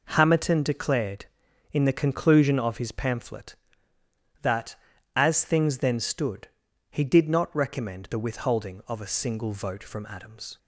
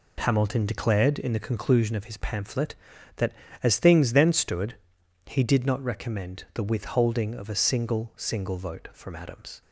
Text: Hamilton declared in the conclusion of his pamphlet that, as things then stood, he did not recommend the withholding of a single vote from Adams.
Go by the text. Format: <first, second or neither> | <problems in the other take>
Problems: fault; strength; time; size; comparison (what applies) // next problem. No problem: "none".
first | says "single" twice; at 8.1 s